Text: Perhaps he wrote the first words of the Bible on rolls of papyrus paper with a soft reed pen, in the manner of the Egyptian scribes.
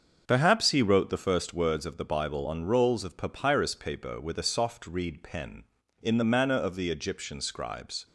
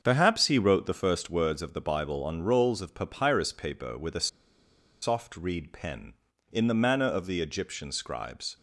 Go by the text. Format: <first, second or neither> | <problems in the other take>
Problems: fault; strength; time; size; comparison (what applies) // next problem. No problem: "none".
first | starts louder than the rest; until 1.0 s; 7 dB; also in the first // pauses between "a" and "soft"; noticeable; at 4.2 s; 0.74 s long